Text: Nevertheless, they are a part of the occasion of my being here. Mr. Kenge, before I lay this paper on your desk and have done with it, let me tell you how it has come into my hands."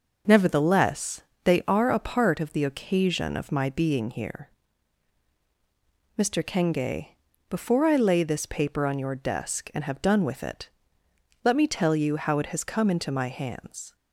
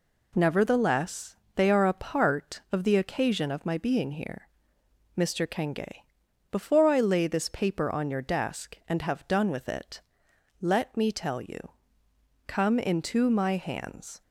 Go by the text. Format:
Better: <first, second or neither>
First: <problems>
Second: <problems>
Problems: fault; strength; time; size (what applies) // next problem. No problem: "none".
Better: first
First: none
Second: skips "how it has"; at 12.0 s